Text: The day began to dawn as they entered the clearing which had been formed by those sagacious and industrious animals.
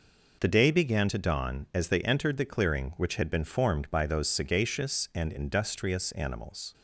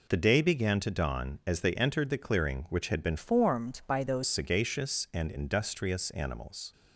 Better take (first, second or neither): first